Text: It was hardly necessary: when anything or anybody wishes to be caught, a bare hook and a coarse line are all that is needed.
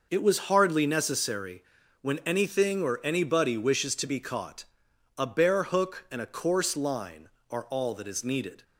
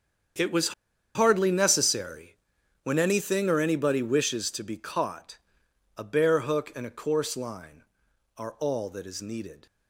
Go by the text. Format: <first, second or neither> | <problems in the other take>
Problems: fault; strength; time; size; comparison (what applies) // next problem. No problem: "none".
first | starts louder than the rest; strong; until 1.8 s; 7.5 dB // pauses between "was" and "hardly"; at 0.7 s; 0.43 s long